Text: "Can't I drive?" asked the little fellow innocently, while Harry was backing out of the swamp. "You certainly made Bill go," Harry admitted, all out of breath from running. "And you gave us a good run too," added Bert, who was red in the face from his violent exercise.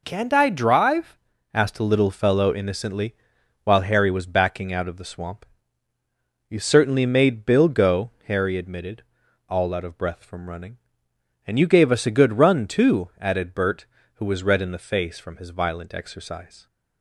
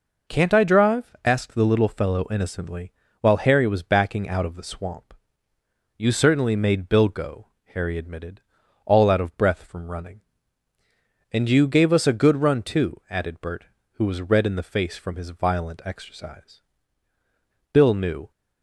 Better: first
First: none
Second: goes on to say "Bill knew"; from 17.7 s on; 0.58 s long

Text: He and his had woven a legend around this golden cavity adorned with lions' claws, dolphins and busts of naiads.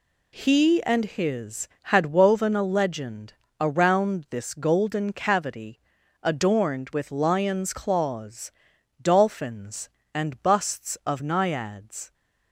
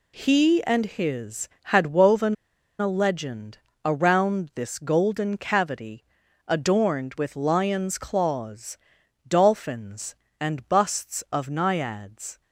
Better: first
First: pauses between "legend" and "around"; slight; at 3.3 s; 0.26 s long // pauses between "cavity" and "adorned"; noticeable; at 5.7 s; 0.46 s long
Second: pauses between "woven" and "a"; at 2.3 s; 0.45 s long // pauses between "legend" and "around"; slight; at 3.5 s; 0.26 s long // pauses between "cavity" and "adorned"; noticeable; at 6.0 s; 0.46 s long

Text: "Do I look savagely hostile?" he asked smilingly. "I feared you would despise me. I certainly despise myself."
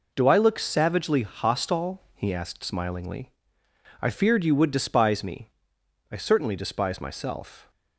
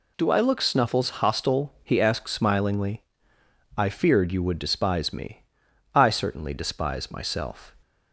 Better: first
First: none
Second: says "snuffles" for "savagely"; at 0.6 s

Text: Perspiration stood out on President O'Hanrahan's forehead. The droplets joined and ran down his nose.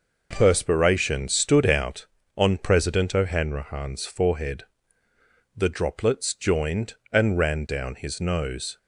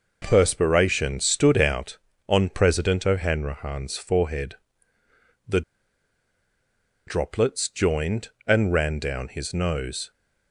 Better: first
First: none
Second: pauses between "The" and "droplets"; strong; at 5.6 s; 1.4 s long

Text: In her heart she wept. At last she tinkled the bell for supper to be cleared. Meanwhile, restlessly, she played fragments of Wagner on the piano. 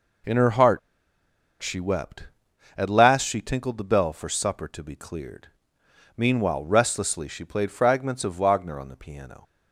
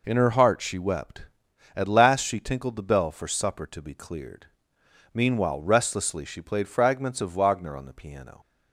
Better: second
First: pauses between "heart" and "she"; noticeable; at 0.7 s; 0.81 s long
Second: none

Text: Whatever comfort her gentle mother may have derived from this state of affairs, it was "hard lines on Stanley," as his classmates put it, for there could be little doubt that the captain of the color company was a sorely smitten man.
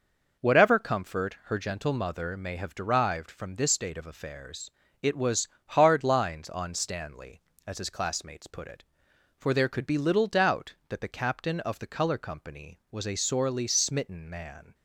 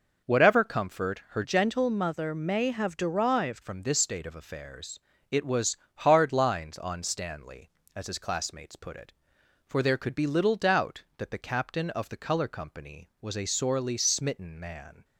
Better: first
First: pauses between "was" and "hard"; slight; at 5.4 s; 0.20 s long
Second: changes voice from "gentle" to "derived"; from 1.4 to 3.6 s; 2.2 s long // pauses between "was" and "hard"; slight; at 5.7 s; 0.20 s long

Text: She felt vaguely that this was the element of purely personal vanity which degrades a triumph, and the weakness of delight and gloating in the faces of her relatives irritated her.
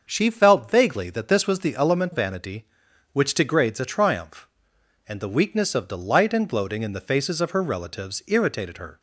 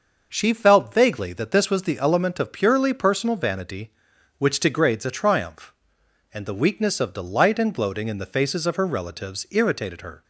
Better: second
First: starts louder than the rest; until 1.1 s; 6 dB // skips "of purely personal"; at 2.1 s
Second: starts louder than the rest; noticeable; until 1.3 s; 6 dB

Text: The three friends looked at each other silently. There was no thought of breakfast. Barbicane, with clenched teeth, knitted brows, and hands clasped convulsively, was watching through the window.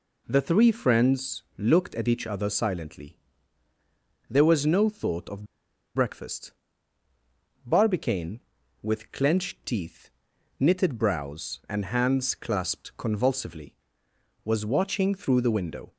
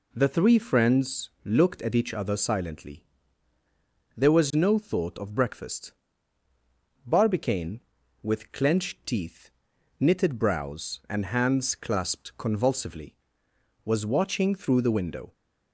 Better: second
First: pauses between "friends" and "looked"; slight; at 1.4 s; 0.16 s long // pauses between "of" and "breakfast"; noticeable; at 5.4 s; 0.51 s long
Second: pauses between "friends" and "looked"; slight; at 1.2 s; 0.16 s long

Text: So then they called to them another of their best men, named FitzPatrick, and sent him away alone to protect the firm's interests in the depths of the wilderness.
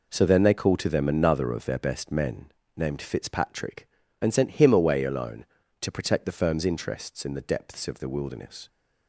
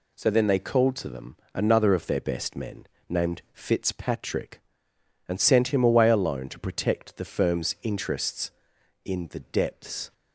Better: first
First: none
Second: pauses between "them" and "another"; slight; at 1.3 s; 0.16 s long // stops before "of the wilderness"; at 10.1 s

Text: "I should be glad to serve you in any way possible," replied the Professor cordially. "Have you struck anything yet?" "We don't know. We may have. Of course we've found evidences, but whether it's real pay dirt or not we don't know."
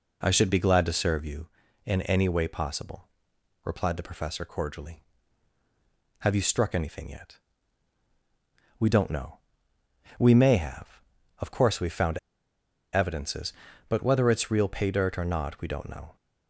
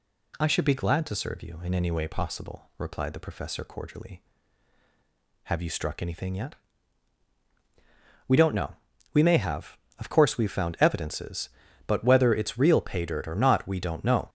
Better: second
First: pauses between "found" and "evidences"; noticeable; at 12.1 s; 0.75 s long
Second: none

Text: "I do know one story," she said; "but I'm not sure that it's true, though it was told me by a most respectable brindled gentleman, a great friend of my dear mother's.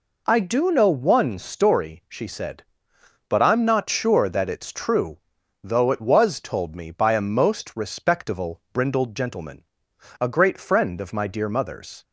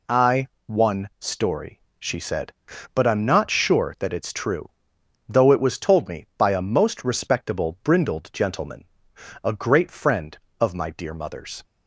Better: first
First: none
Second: skips "do know"; at 0.5 s

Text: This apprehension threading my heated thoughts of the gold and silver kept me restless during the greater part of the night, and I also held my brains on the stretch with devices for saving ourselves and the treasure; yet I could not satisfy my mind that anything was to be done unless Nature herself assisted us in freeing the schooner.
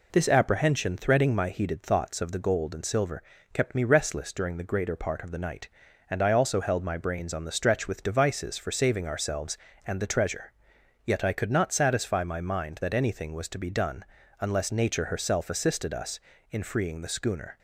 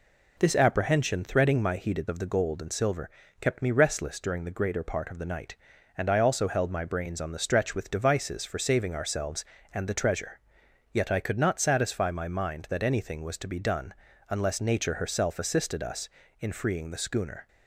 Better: first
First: pauses between "silver" and "kept"; slight; at 3.2 s; 0.30 s long // pauses between "done" and "unless"; at 14.0 s; 0.38 s long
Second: skips "thoughts"; at 2.0 s // pauses between "silver" and "kept"; slight; at 3.0 s; 0.30 s long // pauses between "done" and "unless"; at 13.9 s; 0.38 s long

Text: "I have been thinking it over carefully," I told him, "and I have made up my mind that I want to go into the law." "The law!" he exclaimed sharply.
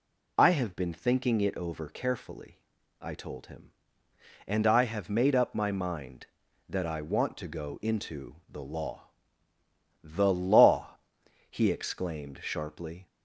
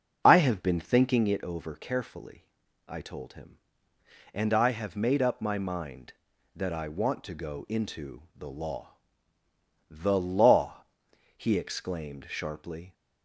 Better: first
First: none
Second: starts louder than the rest; noticeable; until 1.4 s; 6 dB

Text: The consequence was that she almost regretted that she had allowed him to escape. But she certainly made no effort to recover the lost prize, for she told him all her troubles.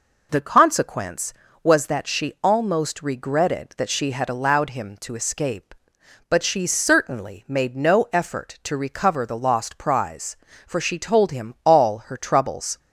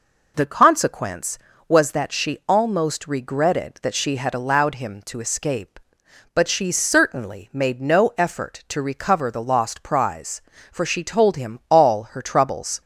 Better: neither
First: none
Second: none

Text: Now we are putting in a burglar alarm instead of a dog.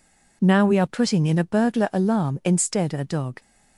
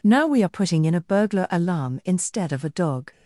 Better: second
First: skips "of"; at 2.9 s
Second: none

